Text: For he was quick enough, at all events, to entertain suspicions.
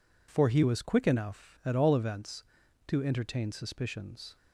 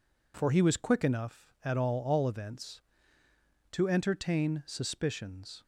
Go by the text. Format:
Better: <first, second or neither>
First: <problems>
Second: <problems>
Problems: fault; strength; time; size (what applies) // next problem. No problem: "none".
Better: first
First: none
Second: says "all" twice; at 2.0 s